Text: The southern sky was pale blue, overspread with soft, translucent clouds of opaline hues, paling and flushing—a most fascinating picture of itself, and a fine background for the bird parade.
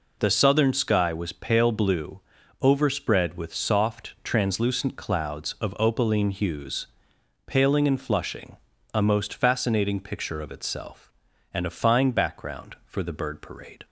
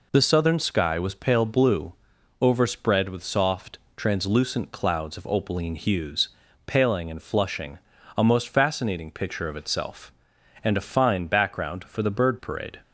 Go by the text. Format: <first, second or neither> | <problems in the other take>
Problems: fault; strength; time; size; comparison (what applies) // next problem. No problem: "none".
neither | none